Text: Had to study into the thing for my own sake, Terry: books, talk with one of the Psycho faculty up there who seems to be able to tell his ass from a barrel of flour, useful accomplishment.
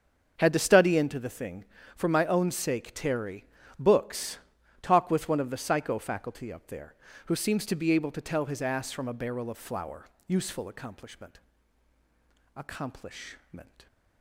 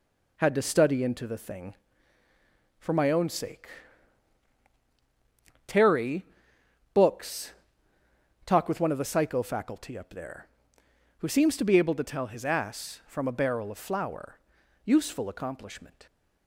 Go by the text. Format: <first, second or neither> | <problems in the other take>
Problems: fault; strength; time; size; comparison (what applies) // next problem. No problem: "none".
second | starts louder than the rest; until 1.3 s; 7 dB // says "accomplishment" twice; at 12.5 s